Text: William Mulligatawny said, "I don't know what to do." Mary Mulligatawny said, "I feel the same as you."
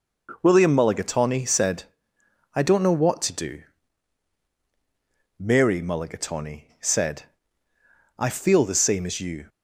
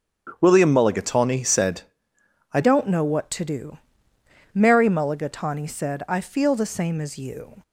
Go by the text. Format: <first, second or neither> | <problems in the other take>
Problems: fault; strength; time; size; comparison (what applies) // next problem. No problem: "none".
first | starts louder than the rest; strong; until 1.4 s; 8.5 dB // changes voice at "don't"; from 2.6 s on; 5.0 s long